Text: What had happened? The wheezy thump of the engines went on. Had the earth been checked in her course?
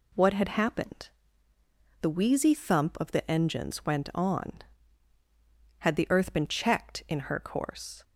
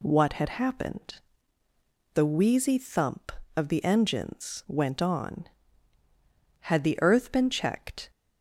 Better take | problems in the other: first | stops before "in her course"; at 8.0 s

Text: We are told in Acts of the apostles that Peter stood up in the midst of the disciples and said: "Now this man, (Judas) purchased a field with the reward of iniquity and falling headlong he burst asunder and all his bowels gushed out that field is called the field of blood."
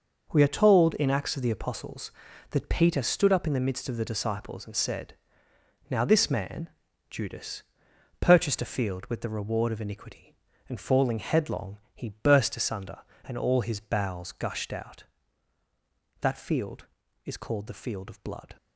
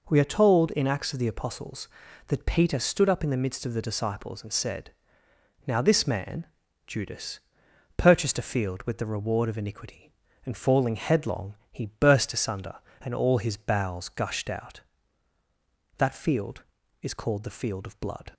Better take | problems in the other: second | gets quieter; strong; throughout; 9 dB // pauses between "headlong" and "he"; slight; at 11.7 s; 0.16 s long; slight in the second

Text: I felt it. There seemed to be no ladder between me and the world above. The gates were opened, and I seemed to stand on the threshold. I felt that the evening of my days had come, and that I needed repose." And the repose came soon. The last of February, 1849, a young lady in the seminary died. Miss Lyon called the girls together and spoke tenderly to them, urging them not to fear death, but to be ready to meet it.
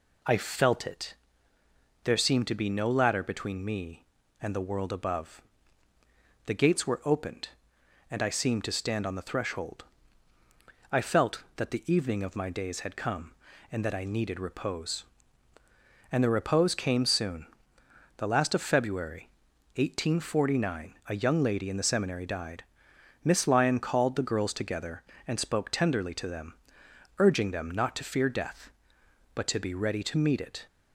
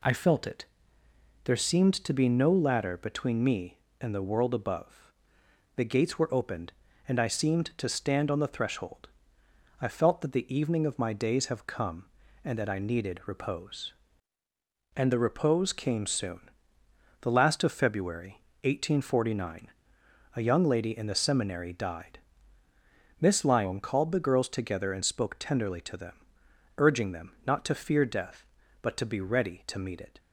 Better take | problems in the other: first | says "have" for "had"; at 11.4 s // pauses between "them" and "not"; slight; at 27.3 s; 0.16 s long

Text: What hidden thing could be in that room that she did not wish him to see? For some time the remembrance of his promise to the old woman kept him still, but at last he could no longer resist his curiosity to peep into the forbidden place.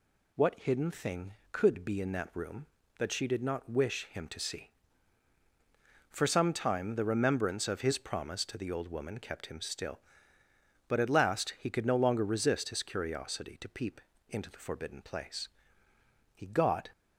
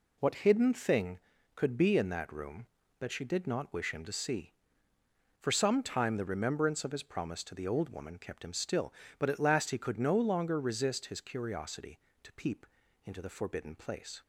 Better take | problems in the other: second | pauses between "peep" and "into"; slight; at 14.0 s; 0.28 s long; also in the second // goes on to say "He got"; from 16.3 s on; 0.56 s long

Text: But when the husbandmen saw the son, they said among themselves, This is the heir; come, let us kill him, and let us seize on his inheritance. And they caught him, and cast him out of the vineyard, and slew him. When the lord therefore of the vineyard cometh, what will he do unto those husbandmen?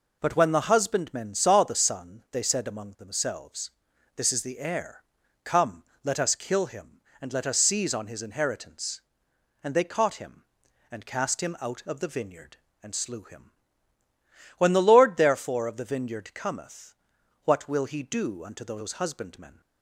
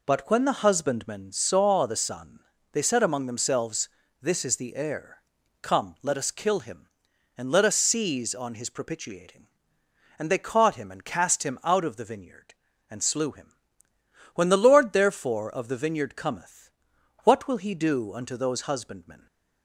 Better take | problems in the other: first | says "propitiating" for "inheritance"; at 8.6 s

